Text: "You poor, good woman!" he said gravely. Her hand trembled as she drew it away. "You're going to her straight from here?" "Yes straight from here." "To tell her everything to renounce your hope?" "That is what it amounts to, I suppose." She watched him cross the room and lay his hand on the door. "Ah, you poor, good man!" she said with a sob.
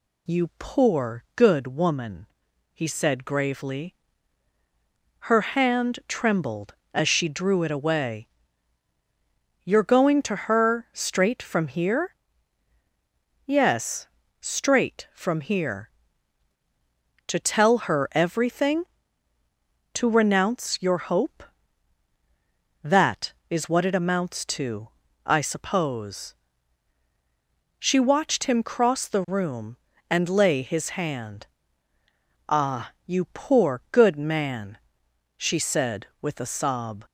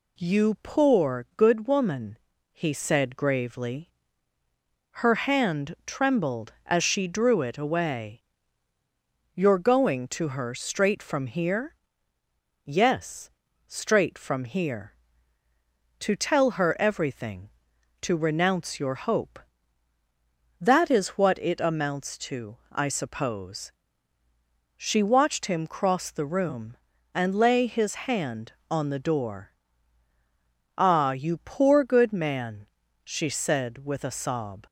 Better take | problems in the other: second | pauses between "Yes" and "straight"; slight; at 14.0 s; 0.32 s long; also in the second // skips "on the door"; at 31.9 s

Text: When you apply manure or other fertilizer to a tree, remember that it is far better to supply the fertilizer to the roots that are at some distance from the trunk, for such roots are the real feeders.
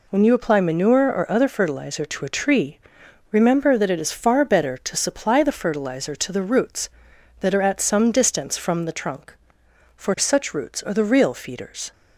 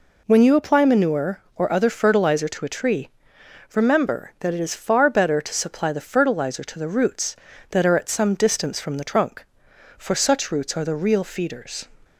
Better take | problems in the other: neither | none

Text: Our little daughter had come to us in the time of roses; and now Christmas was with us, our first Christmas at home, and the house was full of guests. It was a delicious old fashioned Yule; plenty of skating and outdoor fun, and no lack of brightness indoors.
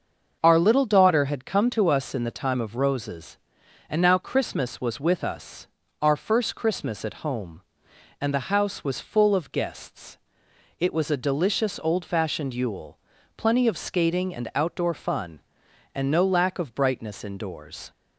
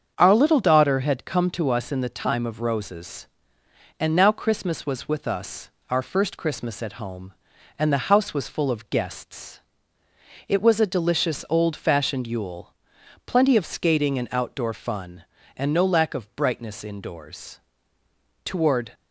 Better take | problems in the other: first | starts louder than the rest; strong; until 1.1 s; 7 dB; also in the first // goes on to say "Toward"; slight; from 18.4 s on; 0.48 s long

